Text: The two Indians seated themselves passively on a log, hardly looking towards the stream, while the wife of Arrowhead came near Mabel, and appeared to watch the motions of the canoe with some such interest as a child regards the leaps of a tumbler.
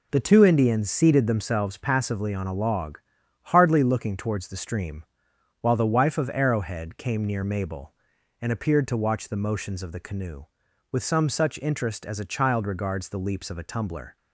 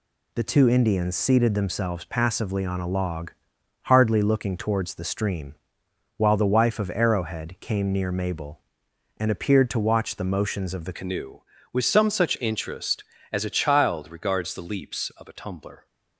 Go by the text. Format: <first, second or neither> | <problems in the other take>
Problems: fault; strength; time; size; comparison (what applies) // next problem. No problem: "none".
first | changes voice at "canoe"; from 10.9 s on; 4.9 s long